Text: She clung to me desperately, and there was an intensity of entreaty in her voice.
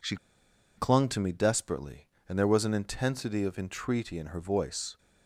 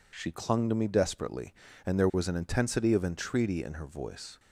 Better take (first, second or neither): second